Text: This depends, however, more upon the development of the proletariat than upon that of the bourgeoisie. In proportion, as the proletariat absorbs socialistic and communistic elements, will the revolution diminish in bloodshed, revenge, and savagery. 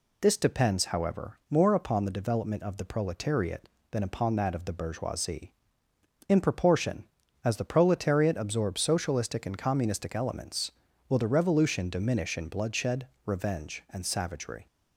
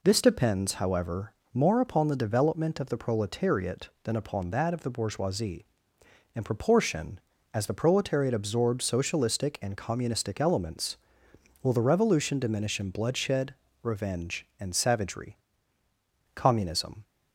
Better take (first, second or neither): first